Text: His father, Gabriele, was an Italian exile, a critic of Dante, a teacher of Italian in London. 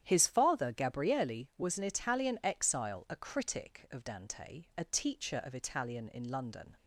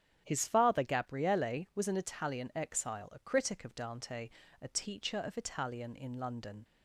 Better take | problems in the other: neither | starts louder than the rest; strong; the same in both

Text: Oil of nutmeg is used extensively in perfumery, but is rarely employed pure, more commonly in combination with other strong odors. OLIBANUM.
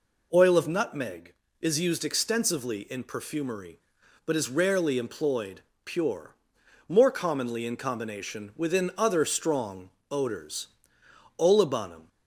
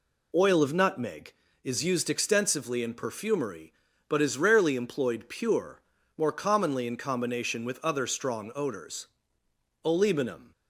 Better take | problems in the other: second | pauses between "employed" and "pure"; slight; at 5.6 s; 0.24 s long // says "within" for "with"; at 8.5 s // pauses between "strong" and "odors"; slight; at 9.9 s; 0.20 s long

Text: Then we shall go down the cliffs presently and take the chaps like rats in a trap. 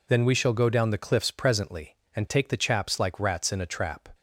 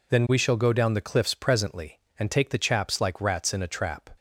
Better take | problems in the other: neither | none

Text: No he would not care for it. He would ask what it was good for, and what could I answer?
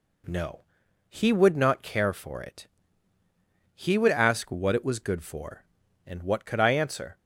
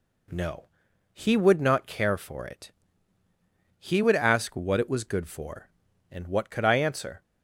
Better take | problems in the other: neither | pauses between "No" and "he"; noticeable; the same in both

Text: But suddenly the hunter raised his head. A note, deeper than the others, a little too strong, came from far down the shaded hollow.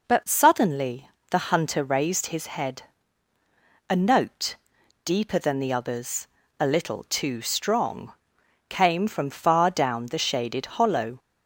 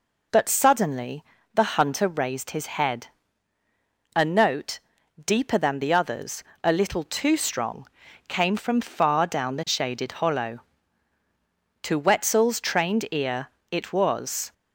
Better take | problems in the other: first | pauses between "suddenly" and "the"; slight; at 1.2 s; 0.30 s long; slight in the first // goes on to say "To Wetzel's trained ear it was"; strong; from 11.8 s on; 2.7 s long

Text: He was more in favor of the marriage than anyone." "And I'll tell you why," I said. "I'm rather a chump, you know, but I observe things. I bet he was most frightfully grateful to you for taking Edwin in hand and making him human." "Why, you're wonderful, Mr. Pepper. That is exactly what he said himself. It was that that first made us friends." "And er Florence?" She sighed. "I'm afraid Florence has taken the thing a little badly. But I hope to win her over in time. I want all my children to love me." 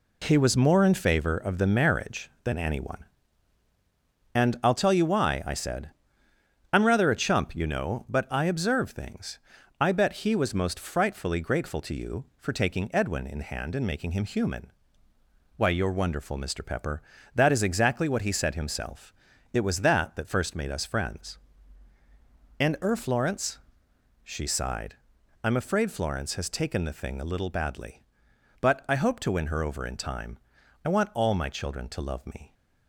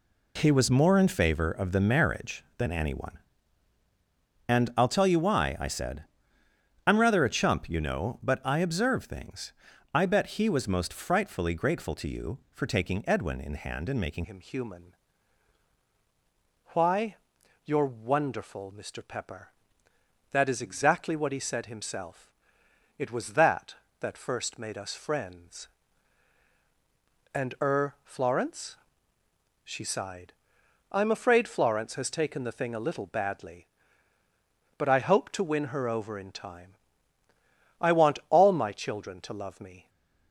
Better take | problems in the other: first | changes voice at "him"; from 14.2 s on; 25.6 s long // stays silent after the last word; slight; from 39.8 s on; 0.5 s long

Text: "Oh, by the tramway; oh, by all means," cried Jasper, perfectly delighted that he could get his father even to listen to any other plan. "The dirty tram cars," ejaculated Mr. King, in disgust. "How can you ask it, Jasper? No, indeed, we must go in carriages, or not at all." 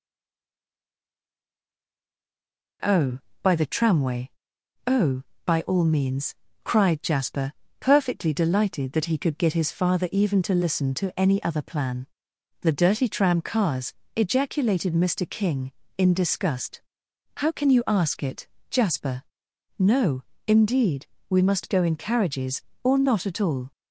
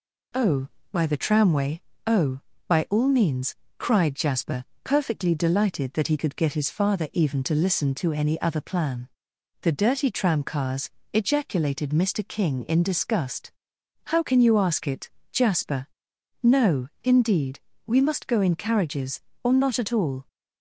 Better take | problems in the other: second | stays silent before the first word; strong; until 2.8 s; 2.8 s long

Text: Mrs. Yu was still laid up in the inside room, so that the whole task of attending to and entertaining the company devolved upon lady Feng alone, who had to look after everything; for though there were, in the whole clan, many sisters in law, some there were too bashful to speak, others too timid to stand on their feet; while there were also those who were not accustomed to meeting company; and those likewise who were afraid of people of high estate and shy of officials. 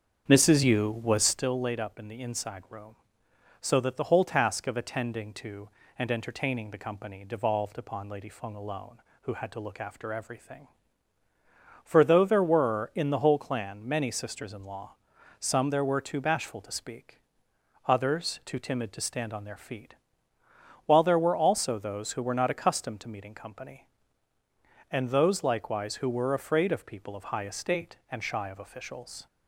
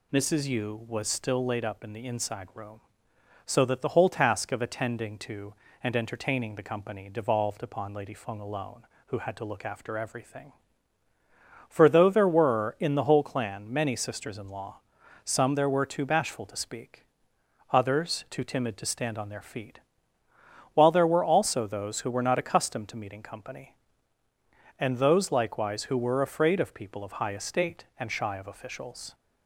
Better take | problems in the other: second | starts louder than the rest; strong; until 1.4 s; 7.5 dB

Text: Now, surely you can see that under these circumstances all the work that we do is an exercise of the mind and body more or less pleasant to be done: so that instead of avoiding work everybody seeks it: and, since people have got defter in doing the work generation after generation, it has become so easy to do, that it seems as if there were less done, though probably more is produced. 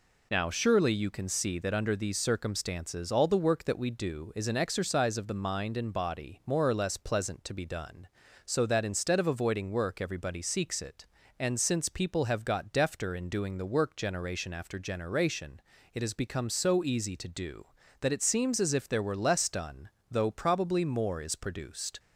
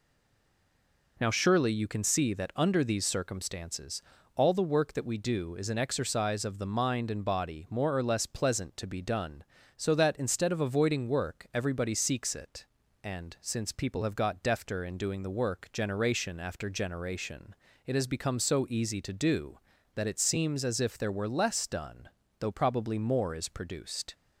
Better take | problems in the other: first | stays silent before the first word; until 1.1 s; 1.1 s long // pauses between "circumstances" and "all"; slight; at 4.0 s; 0.34 s long

